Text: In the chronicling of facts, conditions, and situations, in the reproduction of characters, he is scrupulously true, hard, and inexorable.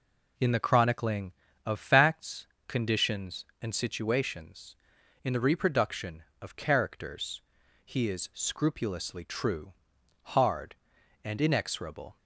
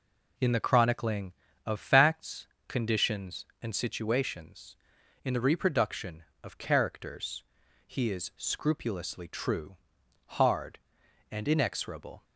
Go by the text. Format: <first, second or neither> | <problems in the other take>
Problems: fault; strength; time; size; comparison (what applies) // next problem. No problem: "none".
neither | none